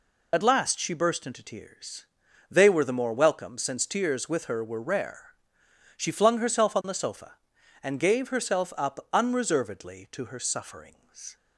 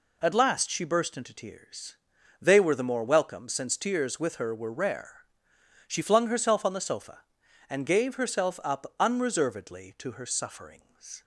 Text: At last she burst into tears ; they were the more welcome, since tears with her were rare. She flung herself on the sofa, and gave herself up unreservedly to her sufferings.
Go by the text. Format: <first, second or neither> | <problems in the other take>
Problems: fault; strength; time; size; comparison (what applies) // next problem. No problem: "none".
second | loses the start of "At"; at 0.3 s; 35 ms